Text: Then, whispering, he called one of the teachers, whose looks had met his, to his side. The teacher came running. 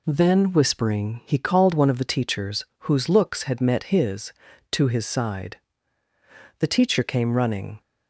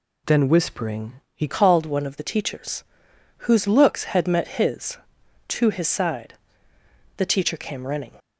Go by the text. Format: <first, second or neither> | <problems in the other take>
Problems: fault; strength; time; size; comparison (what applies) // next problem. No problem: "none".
first | changes voice at "called"; from 1.4 s on; 6.7 s long